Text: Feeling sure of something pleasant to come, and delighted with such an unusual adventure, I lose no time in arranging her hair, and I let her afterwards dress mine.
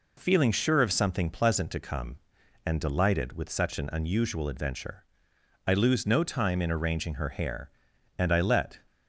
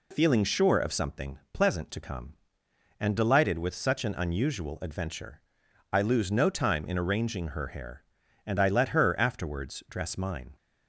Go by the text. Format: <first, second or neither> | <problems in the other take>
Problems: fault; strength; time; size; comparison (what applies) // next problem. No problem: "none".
second | stops before "her afterwards dress mine"; at 8.8 s